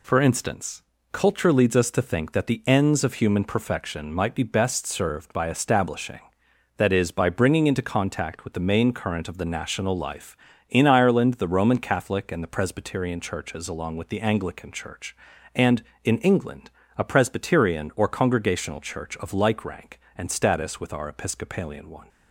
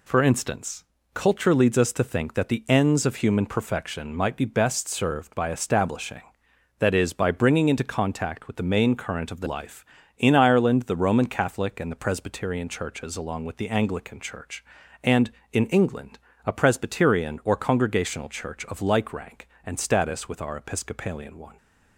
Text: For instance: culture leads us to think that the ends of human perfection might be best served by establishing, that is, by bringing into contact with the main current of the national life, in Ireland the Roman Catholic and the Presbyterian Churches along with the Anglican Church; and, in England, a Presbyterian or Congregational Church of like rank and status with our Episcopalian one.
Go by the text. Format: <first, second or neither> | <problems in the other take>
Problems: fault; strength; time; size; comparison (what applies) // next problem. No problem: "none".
first | skips "national"; at 9.4 s